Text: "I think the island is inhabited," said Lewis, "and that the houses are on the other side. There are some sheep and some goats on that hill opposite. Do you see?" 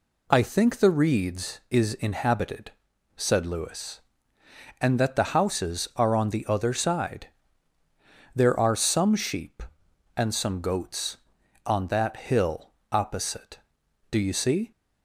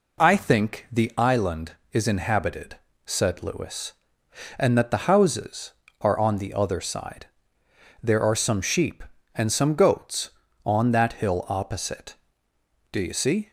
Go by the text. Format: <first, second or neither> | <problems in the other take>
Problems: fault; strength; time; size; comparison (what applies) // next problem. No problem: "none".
second | says "reeds" for "island"; at 0.8 s // pauses between "hill" and "opposite"; slight; at 12.7 s; 0.18 s long